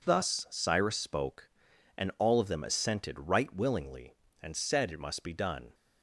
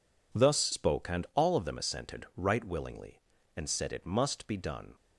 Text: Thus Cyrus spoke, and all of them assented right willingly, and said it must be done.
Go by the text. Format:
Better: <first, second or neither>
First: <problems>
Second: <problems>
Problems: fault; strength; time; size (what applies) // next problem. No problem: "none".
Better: first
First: none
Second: skips "Cyrus"; at 0.7 s